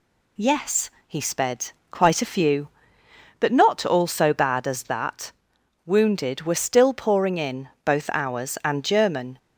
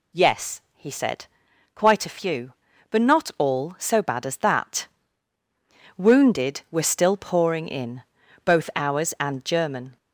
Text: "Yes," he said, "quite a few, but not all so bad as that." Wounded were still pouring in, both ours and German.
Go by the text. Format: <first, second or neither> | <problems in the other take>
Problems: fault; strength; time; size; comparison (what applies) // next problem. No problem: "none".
second | says "sped" for "said"; at 1.2 s